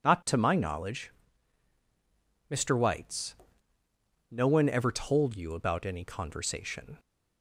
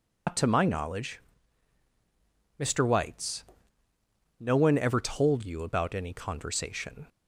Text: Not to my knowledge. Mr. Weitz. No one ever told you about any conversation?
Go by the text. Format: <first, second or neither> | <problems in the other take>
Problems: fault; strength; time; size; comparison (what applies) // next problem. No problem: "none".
first | loses the start of "Not"; at 0.2 s; 90 ms